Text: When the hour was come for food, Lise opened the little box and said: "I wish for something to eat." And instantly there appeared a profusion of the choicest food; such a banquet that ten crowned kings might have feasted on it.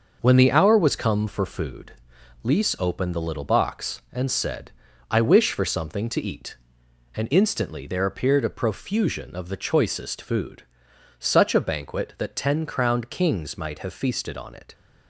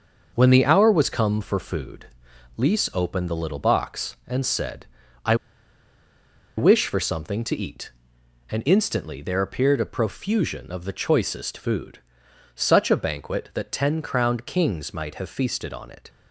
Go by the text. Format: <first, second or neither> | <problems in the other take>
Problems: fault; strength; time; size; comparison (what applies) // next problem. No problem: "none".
first | starts louder than the rest; noticeable; until 1.3 s; 6 dB; noticeable in the first // pauses between "I" and "wish"; at 5.3 s; 1.2 s long